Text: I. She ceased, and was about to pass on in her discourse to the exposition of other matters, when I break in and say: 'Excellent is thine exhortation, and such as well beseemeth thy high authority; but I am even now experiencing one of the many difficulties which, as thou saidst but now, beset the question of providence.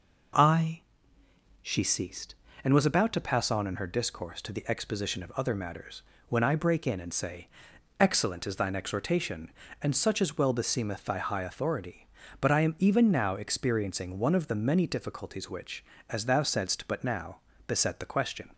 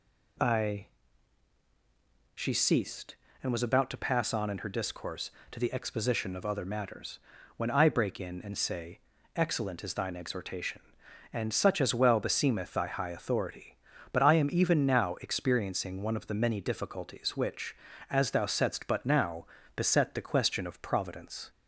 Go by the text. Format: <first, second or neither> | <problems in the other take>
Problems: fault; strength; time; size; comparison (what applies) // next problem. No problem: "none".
second | stops before "of providence"; at 18.5 s